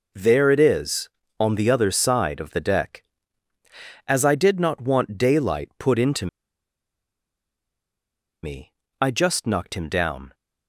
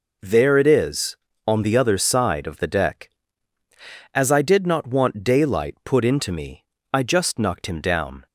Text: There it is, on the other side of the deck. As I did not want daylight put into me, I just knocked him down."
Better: second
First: pauses between "into" and "me"; strong; at 6.2 s; 2.1 s long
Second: none

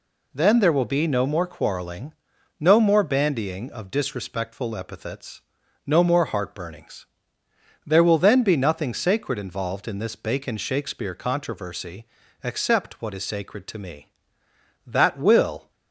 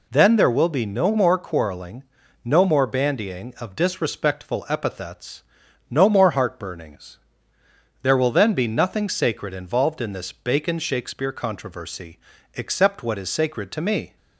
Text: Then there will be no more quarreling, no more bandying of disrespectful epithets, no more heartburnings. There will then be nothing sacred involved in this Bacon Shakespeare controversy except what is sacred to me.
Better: second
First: pauses between "controversy" and "except"; slight; at 12.0 s; 0.36 s long // goes on to say "That will"; noticeable; from 14.8 s on; 0.84 s long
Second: pauses between "controversy" and "except"; slight; at 12.1 s; 0.36 s long

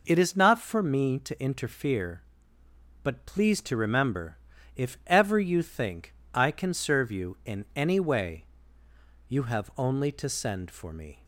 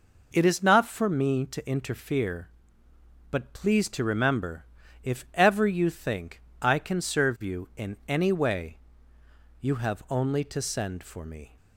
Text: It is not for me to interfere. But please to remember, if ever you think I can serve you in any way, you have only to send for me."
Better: neither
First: pauses between "think" and "I"; slight; at 6.1 s; 0.22 s long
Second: pauses between "think" and "I"; slight; at 6.4 s; 0.22 s long

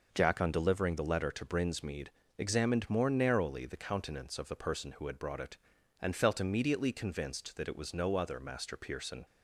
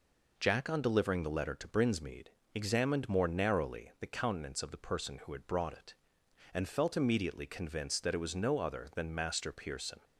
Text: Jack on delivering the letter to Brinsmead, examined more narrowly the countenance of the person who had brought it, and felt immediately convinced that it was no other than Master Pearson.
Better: second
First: skips "than"; at 8.3 s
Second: none

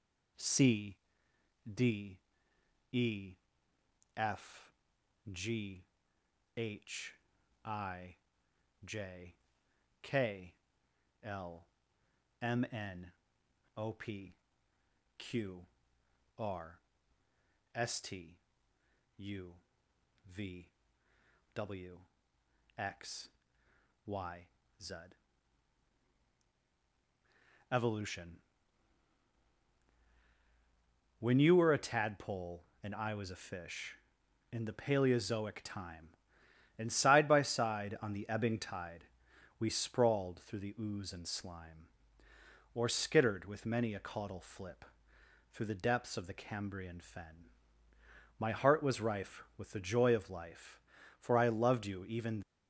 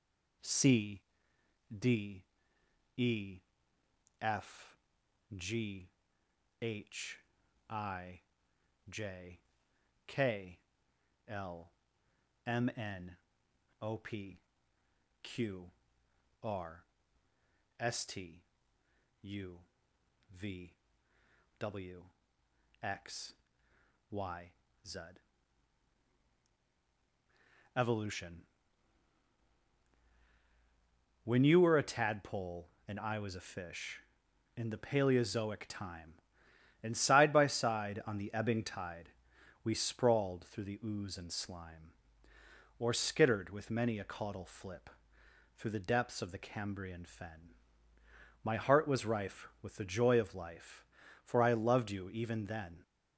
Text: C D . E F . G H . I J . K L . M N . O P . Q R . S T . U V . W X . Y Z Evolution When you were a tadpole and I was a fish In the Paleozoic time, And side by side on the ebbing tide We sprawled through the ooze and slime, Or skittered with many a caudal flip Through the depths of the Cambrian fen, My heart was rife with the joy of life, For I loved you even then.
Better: second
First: pauses between "C" and "D"; noticeable; at 0.9 s; 0.76 s long // pauses between "E" and "F"; noticeable; at 3.3 s; 0.82 s long // pauses between "G" and "H"; noticeable; at 5.8 s; 0.72 s long // pauses between "I" and "J"; noticeable; at 8.1 s; 0.70 s long // pauses between "K" and "L"; noticeable; at 10.5 s; 0.68 s long // pauses between "Q" and "R"; noticeable; at 15.6 s; 0.78 s long // pauses between "U" and "V"; noticeable; at 19.5 s; 0.74 s long // pauses between "W" and "X"; noticeable; at 21.9 s; 0.80 s long // pauses between "Y" and "Z"; at 24.4 s; 0.38 s long // pauses between "Z" and "Evolution"; strong; at 24.9 s; 2.7 s long // pauses between "Evolution" and "When"; strong; at 28.3 s; 2.8 s long // pauses between "tide" and "We"; noticeable; at 39.0 s; 0.54 s long // pauses between "flip" and "Through"; noticeable; at 44.8 s; 0.66 s long // stops before "then"; at 52.4 s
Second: pauses between "C" and "D"; noticeable; at 1.0 s; 0.76 s long // pauses between "E" and "F"; noticeable; at 3.3 s; 0.82 s long // pauses between "G" and "H"; noticeable; at 5.8 s; 0.72 s long // pauses between "I" and "J"; noticeable; at 8.1 s; 0.70 s long // pauses between "K" and "L"; noticeable; at 10.5 s; 0.68 s long // pauses between "Q" and "R"; noticeable; at 15.6 s; 0.78 s long // pauses between "U" and "V"; noticeable; at 19.5 s; 0.74 s long // pauses between "W" and "X"; noticeable; at 22.0 s; 0.80 s long // pauses between "Y" and "Z"; at 24.4 s; 0.38 s long // pauses between "Z" and "Evolution"; strong; at 24.9 s; 2.7 s long // pauses between "Evolution" and "When"; strong; at 28.4 s; 2.8 s long // pauses between "tide" and "We"; noticeable; at 39.0 s; 0.54 s long // pauses between "flip" and "Through"; noticeable; at 44.8 s; 0.66 s long

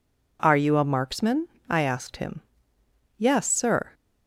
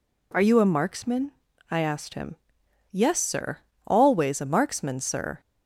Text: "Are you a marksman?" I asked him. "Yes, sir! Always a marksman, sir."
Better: second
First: stops before "Always a marksman sir"; at 3.9 s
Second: none

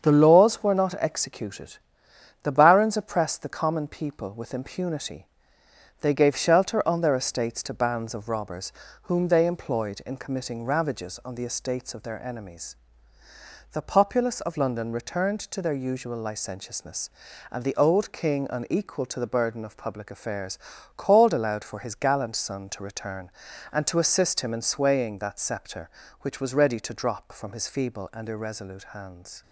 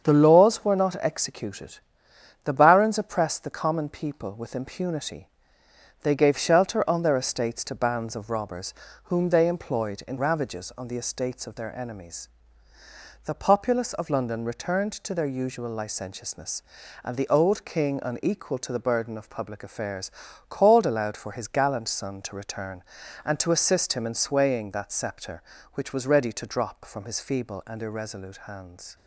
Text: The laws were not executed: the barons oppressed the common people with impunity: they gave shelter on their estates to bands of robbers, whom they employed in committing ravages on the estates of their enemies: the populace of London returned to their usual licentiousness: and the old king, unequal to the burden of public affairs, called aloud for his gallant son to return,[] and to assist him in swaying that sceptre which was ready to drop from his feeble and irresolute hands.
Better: first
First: starts louder than the rest; strong; until 1.1 s; 7 dB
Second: starts louder than the rest; strong; until 1.1 s; 7 dB // skips "committing"; at 10.1 s

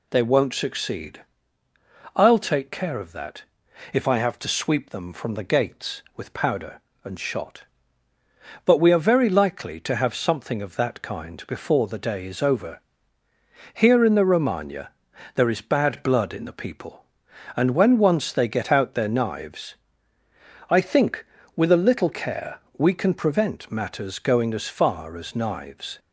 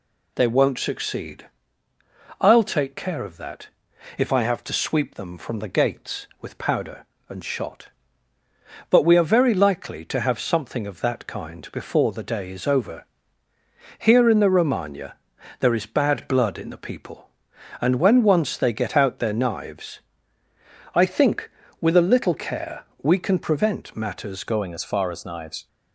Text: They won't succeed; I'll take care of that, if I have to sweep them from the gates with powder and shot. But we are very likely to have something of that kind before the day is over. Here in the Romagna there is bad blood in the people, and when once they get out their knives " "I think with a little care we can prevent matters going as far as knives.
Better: first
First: pauses between "Romagna" and "there"; at 14.8 s; 0.44 s long // pauses between "care" and "we"; slight; at 22.5 s; 0.18 s long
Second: pauses between "Romagna" and "there"; at 15.1 s; 0.44 s long // pauses between "care" and "we"; slight; at 22.8 s; 0.18 s long // changes voice at "going"; from 24.4 s on; 1.2 s long

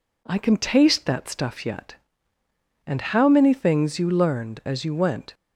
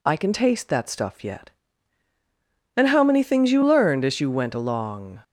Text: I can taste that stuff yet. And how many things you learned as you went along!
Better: second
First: stops before "along"; at 5.3 s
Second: none

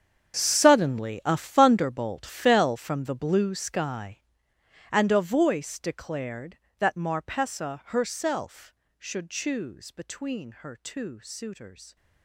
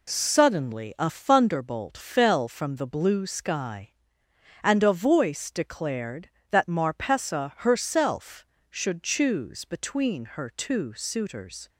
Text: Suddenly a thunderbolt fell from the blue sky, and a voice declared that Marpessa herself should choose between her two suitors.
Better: second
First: gets quieter; strong; throughout; 17 dB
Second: none

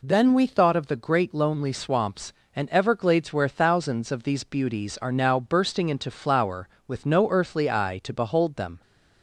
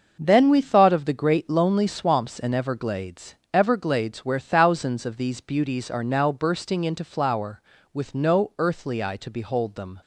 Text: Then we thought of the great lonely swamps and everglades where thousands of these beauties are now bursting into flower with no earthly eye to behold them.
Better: first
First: none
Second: starts louder than the rest; noticeable; until 1.2 s; 6 dB // says "everglades" twice; at 3.5 s

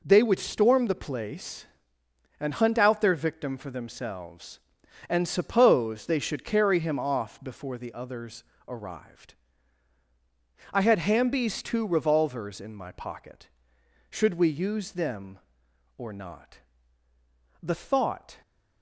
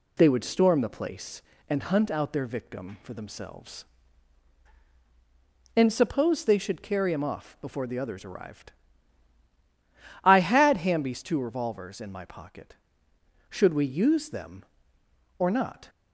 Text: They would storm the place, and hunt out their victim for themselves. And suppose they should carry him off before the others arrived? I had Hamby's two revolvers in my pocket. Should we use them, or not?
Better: second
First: pauses between "others" and "arrived"; slight; at 8.4 s; 0.24 s long // goes on to say "The thought"; noticeable; from 17.6 s on; 0.80 s long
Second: none

